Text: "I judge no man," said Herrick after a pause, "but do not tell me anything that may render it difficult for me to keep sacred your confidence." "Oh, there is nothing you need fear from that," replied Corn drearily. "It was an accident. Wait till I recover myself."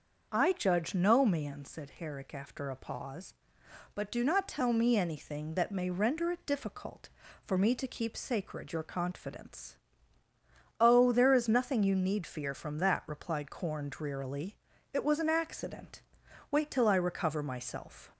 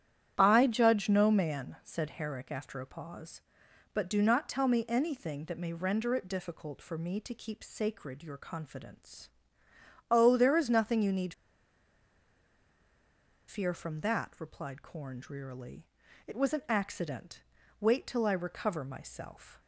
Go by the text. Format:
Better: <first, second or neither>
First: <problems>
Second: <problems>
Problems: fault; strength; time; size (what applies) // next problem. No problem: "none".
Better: first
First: starts louder than the rest; until 1.3 s; 6.5 dB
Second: starts louder than the rest; strong; until 1.3 s; 10.5 dB // pauses between "need" and "fear"; strong; at 11.3 s; 2.1 s long